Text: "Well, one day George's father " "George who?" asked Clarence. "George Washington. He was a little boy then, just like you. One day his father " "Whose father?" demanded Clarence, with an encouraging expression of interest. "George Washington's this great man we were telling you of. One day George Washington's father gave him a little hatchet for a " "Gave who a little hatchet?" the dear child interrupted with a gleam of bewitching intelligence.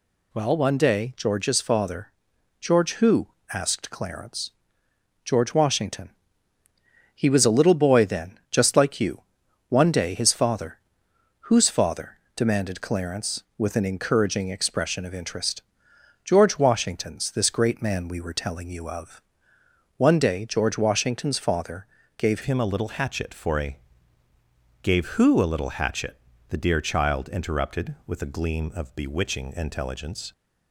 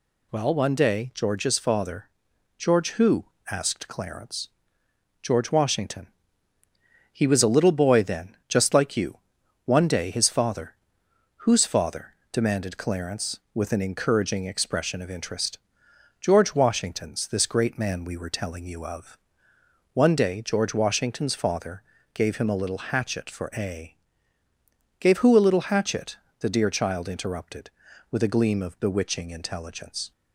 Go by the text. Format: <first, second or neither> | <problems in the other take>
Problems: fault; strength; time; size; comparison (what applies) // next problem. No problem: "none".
second | pauses between "father" and "gave"; slight; at 21.8 s; 0.28 s long; slight in the second // changes voice at "him"; from 22.4 s on; 7.9 s long